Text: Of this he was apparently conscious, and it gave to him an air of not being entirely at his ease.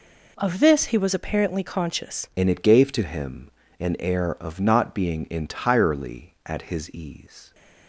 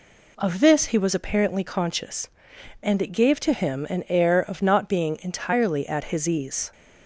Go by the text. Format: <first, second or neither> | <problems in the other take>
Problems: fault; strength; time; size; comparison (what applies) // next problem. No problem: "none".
second | changes voice at "and"; from 2.3 s on; 5.2 s long // pauses between "him" and "an"; slight; at 3.5 s; 0.28 s long